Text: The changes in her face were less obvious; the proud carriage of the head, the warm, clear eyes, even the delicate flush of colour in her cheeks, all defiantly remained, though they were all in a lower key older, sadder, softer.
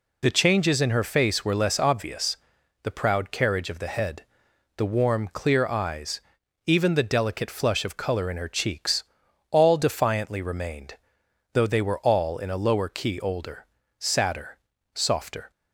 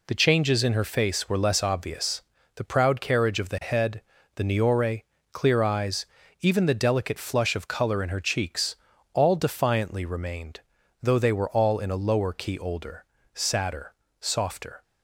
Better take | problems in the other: first | says "niore" for "warm"; at 4.4 s

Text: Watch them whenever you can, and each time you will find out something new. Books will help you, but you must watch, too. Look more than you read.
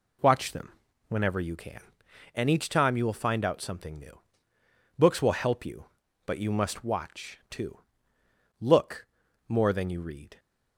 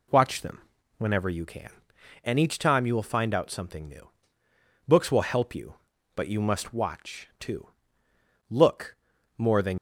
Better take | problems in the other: first | pauses between "them" and "whenever"; slight; at 0.6 s; 0.34 s long; slight in the first // pauses between "Look" and "more"; at 8.9 s; 0.40 s long; also in the first // stops before "you read"; at 9.7 s

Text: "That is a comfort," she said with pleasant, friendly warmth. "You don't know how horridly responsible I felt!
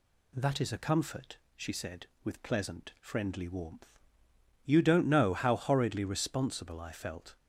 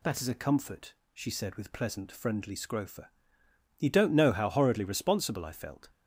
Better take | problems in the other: first | says "scrofa" for "warmth"; at 2.5 s

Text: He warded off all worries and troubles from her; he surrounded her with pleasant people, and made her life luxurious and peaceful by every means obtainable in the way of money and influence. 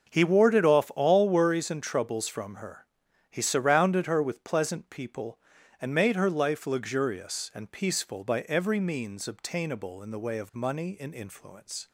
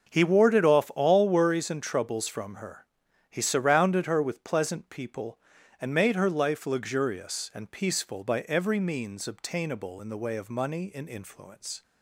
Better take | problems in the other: neither | starts louder than the rest; the same in both

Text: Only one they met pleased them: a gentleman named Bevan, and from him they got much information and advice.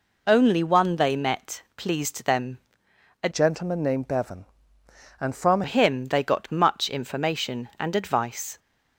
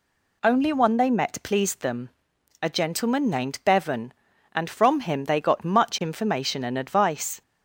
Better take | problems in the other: second | changes voice from "gentleman" to "from"; from 3.3 to 5.6 s; 2.3 s long

